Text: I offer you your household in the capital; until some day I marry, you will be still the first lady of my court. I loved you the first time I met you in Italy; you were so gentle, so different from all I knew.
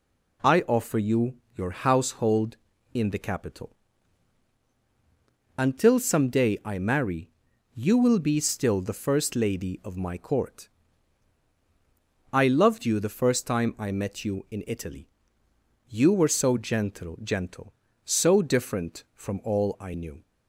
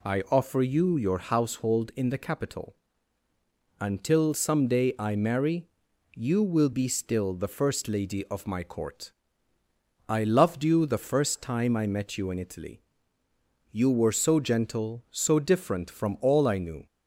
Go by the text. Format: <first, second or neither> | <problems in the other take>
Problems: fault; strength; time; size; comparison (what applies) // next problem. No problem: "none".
second | pauses between "you" and "your"; slight; at 1.3 s; 0.22 s long // says "gentle" twice; at 17.2 s